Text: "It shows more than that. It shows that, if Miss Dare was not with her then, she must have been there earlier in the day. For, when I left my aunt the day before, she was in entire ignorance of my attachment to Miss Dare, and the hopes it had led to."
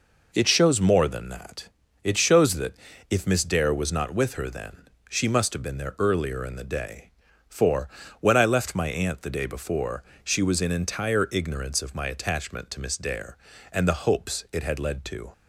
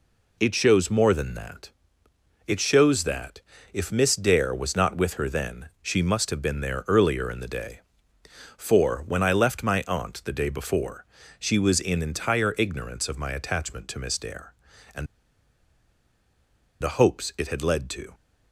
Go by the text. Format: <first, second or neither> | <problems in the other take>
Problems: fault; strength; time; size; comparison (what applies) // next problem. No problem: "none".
first | pauses between "and" and "the"; strong; at 15.0 s; 1.7 s long